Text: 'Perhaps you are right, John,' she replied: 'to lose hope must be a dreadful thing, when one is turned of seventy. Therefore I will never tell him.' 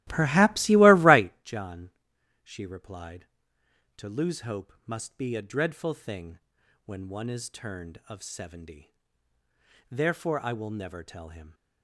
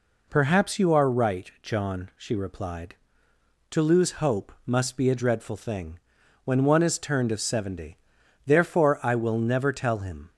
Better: second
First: starts louder than the rest; strong; until 1.4 s; 15 dB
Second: none

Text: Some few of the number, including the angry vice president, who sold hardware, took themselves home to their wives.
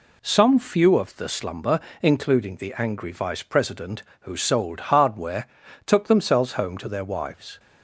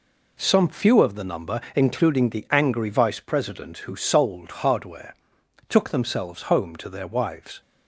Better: second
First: says "slumber" for "number"; at 1.2 s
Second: none

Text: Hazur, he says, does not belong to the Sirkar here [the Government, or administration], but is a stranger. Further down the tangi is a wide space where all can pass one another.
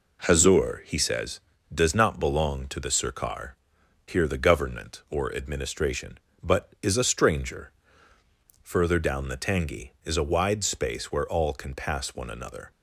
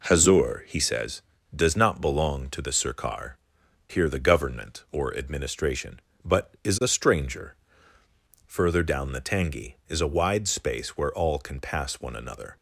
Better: neither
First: pauses between "Sirkar" and "here"; noticeable; at 3.5 s; 0.54 s long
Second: pauses between "Sirkar" and "here"; noticeable; at 3.3 s; 0.54 s long

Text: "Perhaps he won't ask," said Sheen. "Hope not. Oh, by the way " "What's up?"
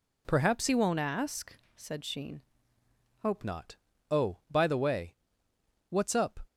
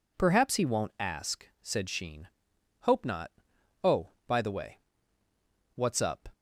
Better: second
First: changes voice from "he" to "Hope"; from 0.6 to 3.4 s; 2.8 s long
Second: none

